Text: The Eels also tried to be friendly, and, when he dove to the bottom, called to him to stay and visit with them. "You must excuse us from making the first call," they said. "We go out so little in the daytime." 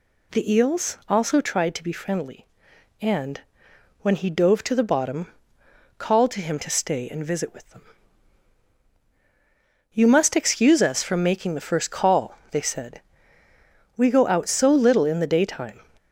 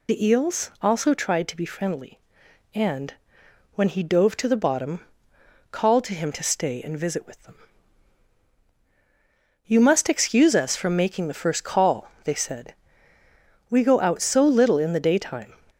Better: first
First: none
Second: loses the start of "The"; at 0.0 s; 45 ms

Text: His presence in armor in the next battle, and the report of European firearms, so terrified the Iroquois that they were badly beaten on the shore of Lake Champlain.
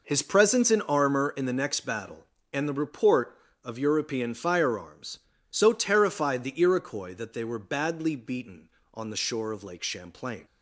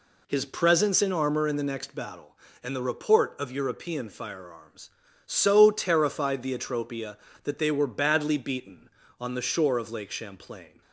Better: first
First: none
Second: says "Atropia" for "Iroquois"; at 6.5 s

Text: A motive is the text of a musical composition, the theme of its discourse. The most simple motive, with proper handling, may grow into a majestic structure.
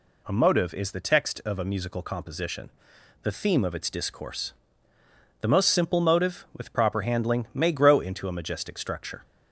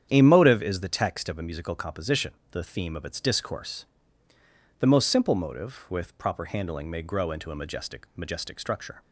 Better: first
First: none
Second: starts louder than the rest; strong; until 1.1 s; 9 dB // says "majestic" twice; at 8.1 s

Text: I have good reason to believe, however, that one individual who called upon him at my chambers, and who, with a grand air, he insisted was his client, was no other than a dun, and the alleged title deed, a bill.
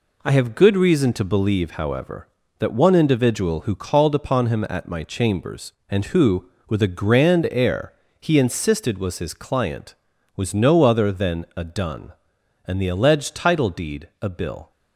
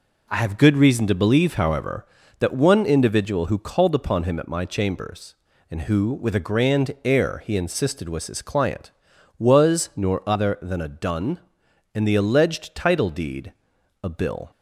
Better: first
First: none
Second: says "nor" for "no"; at 9.9 s

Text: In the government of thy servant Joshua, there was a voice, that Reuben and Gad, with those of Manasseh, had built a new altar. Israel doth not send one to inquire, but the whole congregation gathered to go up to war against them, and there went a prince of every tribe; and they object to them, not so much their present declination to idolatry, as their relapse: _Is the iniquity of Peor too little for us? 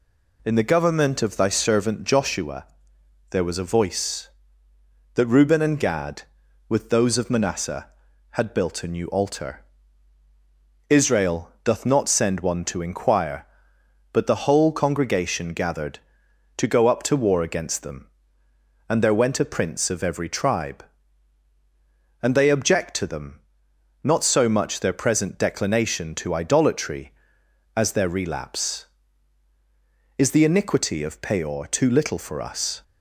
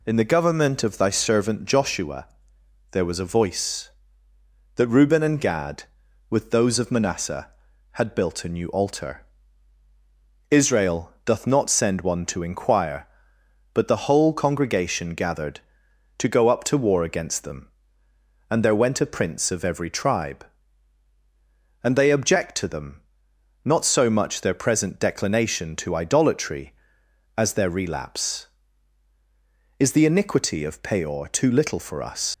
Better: first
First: none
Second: leaves "us" unfinished; at 32.3 s; 95 ms

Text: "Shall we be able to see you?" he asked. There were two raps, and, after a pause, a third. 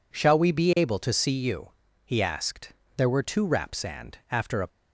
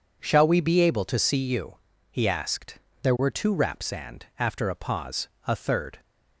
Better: second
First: stops before "pause a third"; at 4.6 s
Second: none

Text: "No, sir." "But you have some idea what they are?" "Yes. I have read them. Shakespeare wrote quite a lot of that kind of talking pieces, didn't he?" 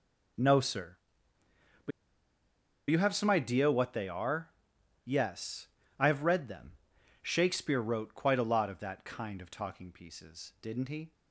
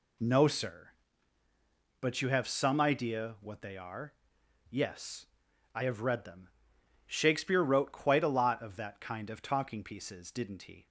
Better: second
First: pauses between "But" and "you"; at 1.9 s; 0.99 s long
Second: none

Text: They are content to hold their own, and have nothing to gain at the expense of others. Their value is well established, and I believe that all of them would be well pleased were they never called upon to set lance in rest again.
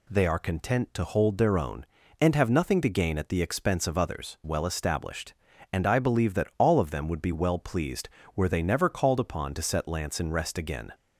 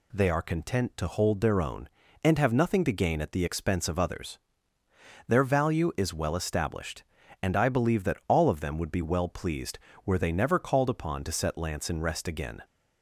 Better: second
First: skips "Their value is"; at 4.4 s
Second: none

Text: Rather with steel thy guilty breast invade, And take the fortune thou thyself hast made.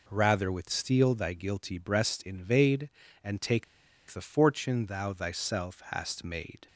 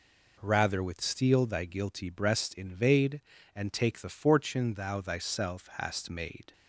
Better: second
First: pauses between "take" and "the"; noticeable; at 3.6 s; 0.46 s long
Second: none

